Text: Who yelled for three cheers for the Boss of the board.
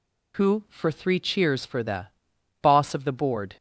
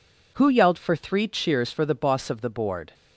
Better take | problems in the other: second | skips "yelled"; at 0.6 s // pauses between "the" and "Boss"; noticeable; at 2.0 s; 0.54 s long

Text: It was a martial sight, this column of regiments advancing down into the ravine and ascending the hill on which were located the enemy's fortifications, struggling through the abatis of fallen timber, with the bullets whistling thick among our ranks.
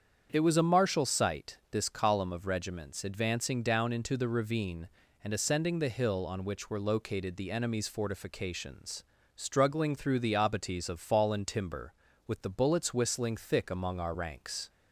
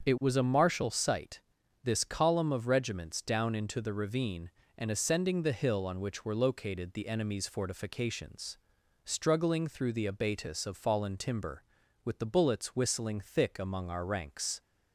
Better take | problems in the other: first | starts louder than the rest; until 1.0 s; 7 dB; strong in the first // skips "advancing"; at 3.2 s

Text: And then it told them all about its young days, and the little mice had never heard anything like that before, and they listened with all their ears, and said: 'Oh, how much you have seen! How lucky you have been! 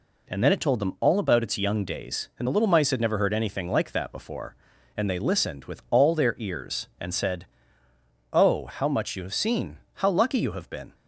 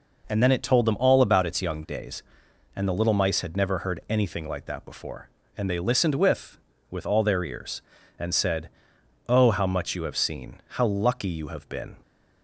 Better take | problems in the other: first | says "with" twice; at 6.9 s

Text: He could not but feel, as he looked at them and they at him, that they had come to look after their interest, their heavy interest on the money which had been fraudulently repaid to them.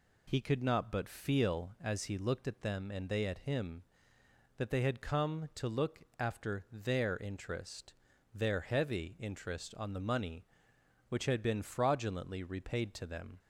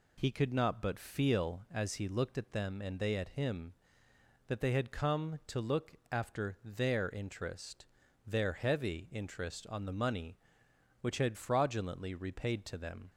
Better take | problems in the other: first | pauses between "look" and "after"; slight; at 5.9 s; 0.16 s long; slight in the first // skips "been"; at 11.3 s

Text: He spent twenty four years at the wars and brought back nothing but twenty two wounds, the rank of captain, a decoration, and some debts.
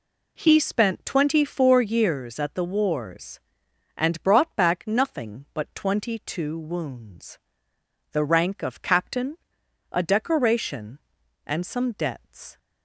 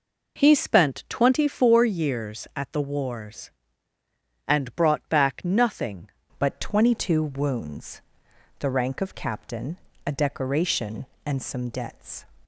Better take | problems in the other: first | changes voice at "but"; from 6.3 s on; 5.9 s long

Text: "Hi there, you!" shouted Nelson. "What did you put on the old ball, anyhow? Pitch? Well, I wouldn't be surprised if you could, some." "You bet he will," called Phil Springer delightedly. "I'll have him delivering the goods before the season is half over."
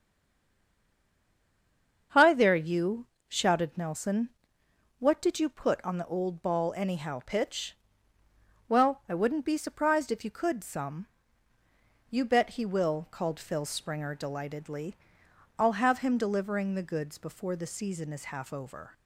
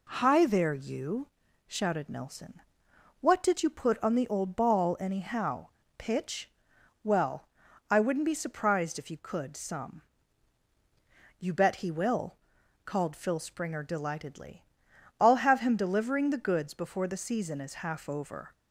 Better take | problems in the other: second | stays silent before the first word; noticeable; until 2.1 s; 2.1 s long // starts louder than the rest; until 3.3 s; 7 dB

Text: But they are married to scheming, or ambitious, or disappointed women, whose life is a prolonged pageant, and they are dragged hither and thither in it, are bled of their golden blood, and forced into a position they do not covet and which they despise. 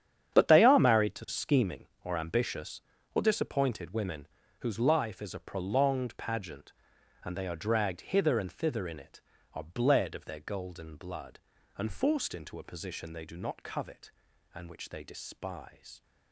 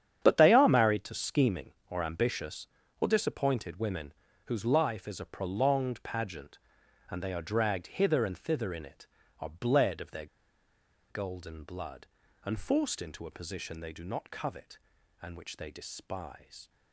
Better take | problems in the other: first | starts louder than the rest; strong; until 1.2 s; 9 dB; strong in the first // pauses between "their" and "golden"; noticeable; at 10.2 s; 0.84 s long

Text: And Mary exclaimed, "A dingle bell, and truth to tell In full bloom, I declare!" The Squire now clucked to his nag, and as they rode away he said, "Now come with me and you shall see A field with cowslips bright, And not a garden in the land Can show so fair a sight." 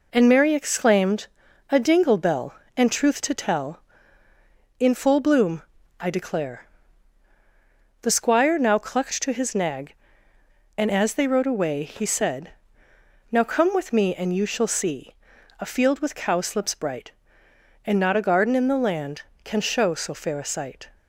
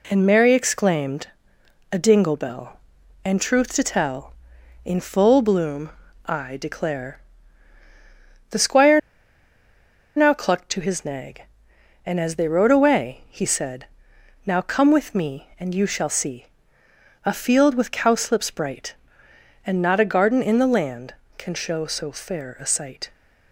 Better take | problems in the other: first | pauses between "Squire" and "now"; at 8.9 s; 1.1 s long // pauses between "see" and "A"; noticeable; at 16.4 s; 0.78 s long; also in the first

